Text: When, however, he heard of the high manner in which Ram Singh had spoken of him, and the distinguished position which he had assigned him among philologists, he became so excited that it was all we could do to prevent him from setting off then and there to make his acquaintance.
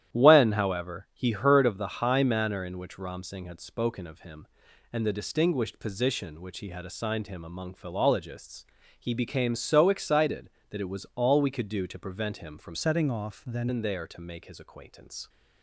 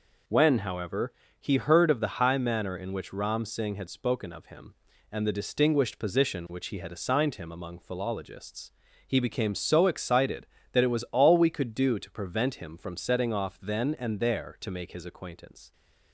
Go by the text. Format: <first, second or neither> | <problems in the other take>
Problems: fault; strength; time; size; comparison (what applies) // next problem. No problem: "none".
second | starts louder than the rest; strong; until 1.1 s; 11 dB // changes voice from "setting" to "then"; from 12.7 to 13.6 s; 0.9 s long